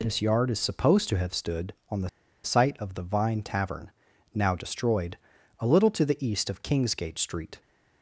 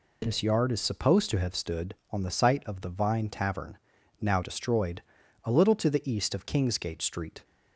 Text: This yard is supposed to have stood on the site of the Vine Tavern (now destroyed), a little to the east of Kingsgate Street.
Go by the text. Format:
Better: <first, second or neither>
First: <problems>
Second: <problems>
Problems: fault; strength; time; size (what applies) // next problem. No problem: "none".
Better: second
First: pauses between "the" and "site"; slight; at 2.0 s; 0.34 s long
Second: none